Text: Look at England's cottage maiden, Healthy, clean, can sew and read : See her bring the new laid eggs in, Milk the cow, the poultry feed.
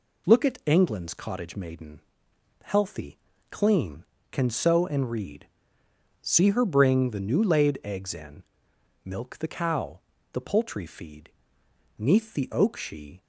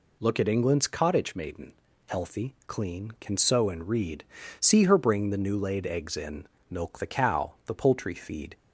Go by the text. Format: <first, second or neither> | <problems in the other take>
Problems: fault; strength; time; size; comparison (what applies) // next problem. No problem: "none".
second | goes on to say "Neath the oak she"; noticeable; from 11.9 s on; 1.2 s long